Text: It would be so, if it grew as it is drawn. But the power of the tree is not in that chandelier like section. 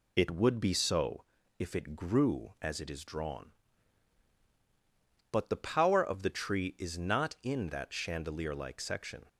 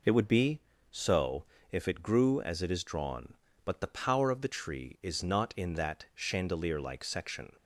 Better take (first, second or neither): neither